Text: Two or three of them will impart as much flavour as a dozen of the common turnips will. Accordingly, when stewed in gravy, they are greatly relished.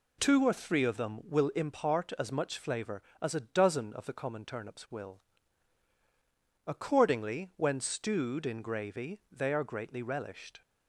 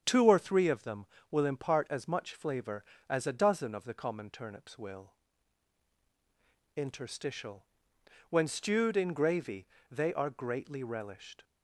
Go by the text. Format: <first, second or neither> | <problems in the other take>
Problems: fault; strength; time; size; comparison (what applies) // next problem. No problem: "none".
first | starts louder than the rest; strong; until 1.0 s; 8 dB // says "Interstitial" for "Accordingly"; at 6.7 s